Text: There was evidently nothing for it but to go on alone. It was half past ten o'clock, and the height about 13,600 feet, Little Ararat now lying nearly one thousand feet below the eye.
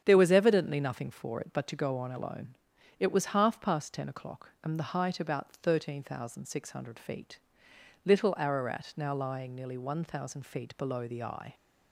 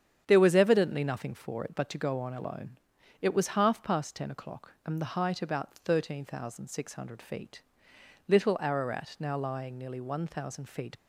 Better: first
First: starts louder than the rest; strong; until 1.0 s; 8.5 dB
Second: starts louder than the rest; strong; until 1.2 s; 8.5 dB // stops before "below the eye"; at 10.9 s

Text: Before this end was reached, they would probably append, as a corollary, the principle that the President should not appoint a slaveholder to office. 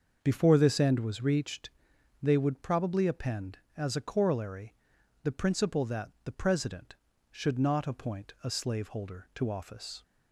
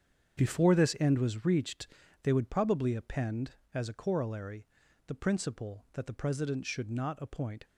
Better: first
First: starts louder than the rest; until 1.2 s; 6.5 dB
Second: starts louder than the rest; strong; until 1.4 s; 7.5 dB // stops before "a slaveholder to office"; at 7.6 s

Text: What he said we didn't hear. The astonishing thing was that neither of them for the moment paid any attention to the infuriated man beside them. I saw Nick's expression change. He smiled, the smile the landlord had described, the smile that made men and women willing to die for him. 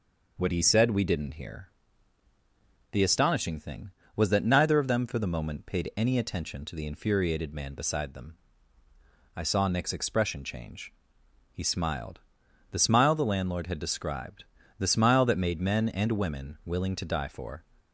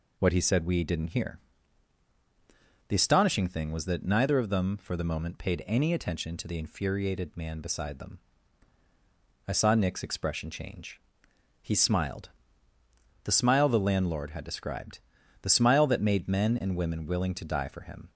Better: second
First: stops before "him"; at 17.8 s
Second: none

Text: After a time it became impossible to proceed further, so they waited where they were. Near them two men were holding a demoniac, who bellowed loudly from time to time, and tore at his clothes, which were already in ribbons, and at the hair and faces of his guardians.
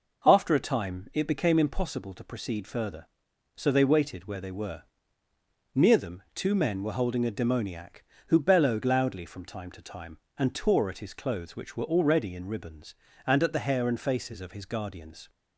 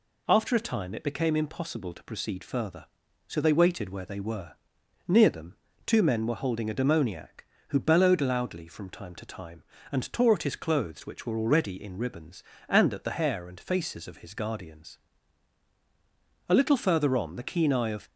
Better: first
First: none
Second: pauses between "them" and "two"; slight; at 5.5 s; 0.30 s long // goes on to say "A little further on the keen eye of"; from 16.4 s on; 1.6 s long

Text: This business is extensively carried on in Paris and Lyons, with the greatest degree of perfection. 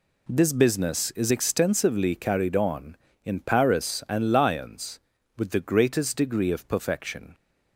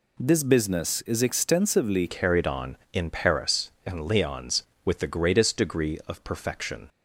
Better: first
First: none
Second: changes voice at "carried"; from 2.0 s on; 4.8 s long

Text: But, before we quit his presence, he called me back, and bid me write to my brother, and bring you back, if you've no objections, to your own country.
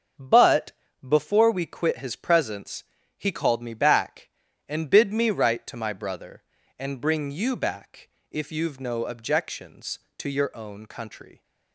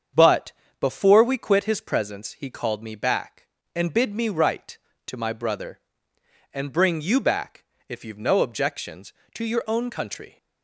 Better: neither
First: starts louder than the rest; strong; until 1.5 s; 7.5 dB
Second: starts louder than the rest; strong; until 1.4 s; 7.5 dB

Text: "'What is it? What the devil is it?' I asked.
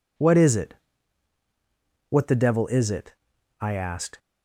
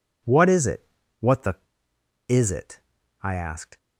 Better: first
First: none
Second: skips "devil"; at 1.9 s

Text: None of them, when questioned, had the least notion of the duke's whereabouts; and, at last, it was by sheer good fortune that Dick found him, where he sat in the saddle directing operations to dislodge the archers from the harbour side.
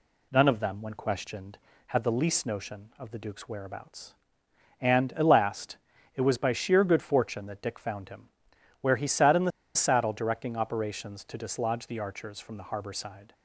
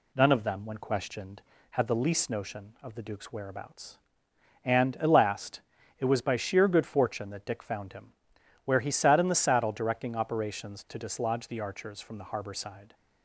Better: second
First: pauses between "the" and "saddle"; slight; at 9.5 s; 0.24 s long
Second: none

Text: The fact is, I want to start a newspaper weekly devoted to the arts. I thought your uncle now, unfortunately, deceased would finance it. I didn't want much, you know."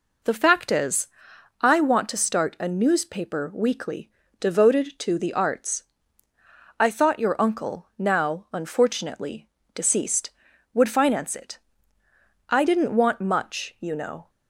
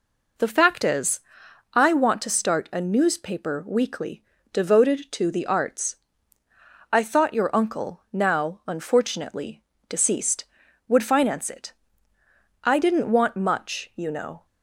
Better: neither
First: pauses between "weekly" and "devoted"; slight; at 4.0 s; 0.30 s long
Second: pauses between "weekly" and "devoted"; slight; at 4.2 s; 0.30 s long

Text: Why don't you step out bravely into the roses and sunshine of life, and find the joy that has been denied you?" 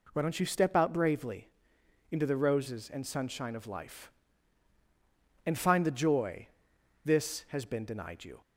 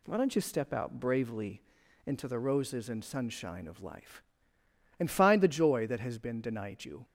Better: second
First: pauses between "bravely" and "into"; noticeable; at 1.4 s; 0.62 s long // says "this" for "that"; at 7.0 s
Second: pauses between "bravely" and "into"; at 1.6 s; 0.44 s long

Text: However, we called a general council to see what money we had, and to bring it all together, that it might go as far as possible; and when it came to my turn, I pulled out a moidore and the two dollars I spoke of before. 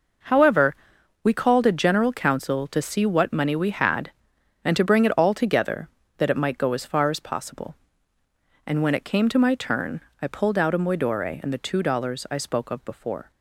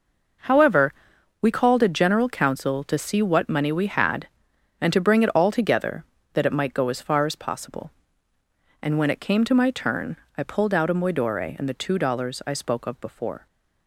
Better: neither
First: none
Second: none

